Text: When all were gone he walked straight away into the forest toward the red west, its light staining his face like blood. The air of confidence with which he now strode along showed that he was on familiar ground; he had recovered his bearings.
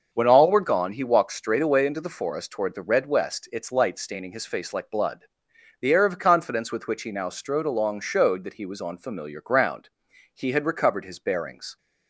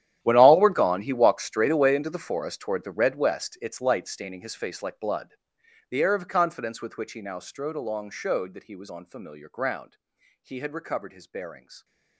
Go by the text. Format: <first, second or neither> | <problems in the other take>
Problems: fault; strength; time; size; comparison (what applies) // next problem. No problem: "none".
first | gets quieter; strong; throughout; 19.5 dB // starts louder than the rest; strong; until 1.2 s; 11 dB; noticeable in the first